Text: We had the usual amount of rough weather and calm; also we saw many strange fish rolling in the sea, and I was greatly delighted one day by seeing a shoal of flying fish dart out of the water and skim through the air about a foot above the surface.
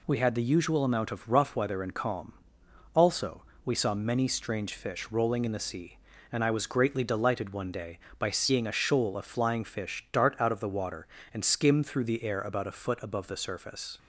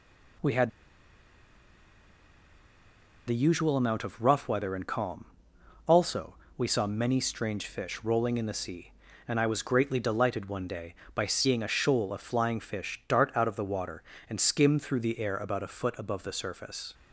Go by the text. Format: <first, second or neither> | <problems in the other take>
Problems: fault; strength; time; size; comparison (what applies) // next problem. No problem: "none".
first | pauses between "had" and "the"; strong; at 0.6 s; 2.5 s long // pauses between "also" and "we"; slight; at 6.3 s; 0.18 s long; slight in the first